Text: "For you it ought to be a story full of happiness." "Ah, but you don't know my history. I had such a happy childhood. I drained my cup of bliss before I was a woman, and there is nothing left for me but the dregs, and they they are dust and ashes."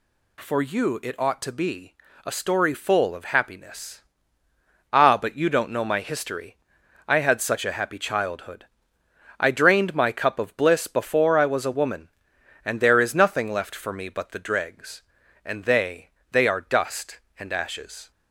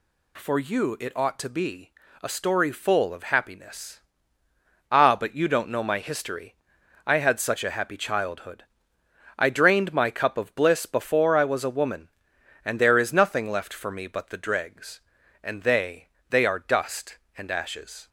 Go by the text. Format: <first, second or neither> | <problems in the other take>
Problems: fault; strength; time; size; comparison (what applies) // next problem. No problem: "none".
neither | pauses between "be" and "a"; slight; the same in both // pauses between "they" and "they"; slight; the same in both